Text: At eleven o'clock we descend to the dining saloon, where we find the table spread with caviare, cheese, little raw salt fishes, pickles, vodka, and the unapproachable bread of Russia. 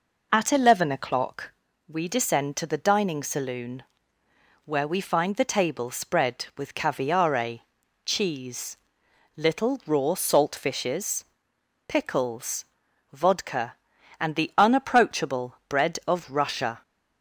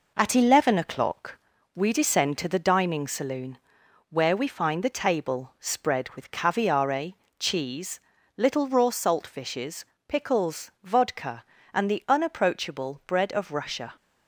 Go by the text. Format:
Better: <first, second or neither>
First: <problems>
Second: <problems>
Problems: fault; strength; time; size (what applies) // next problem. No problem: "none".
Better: first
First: pauses between "o'clock" and "we"; at 1.4 s; 0.38 s long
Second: gets quieter; noticeable; throughout; 4 dB // pauses between "o'clock" and "we"; slight; at 1.3 s; 0.34 s long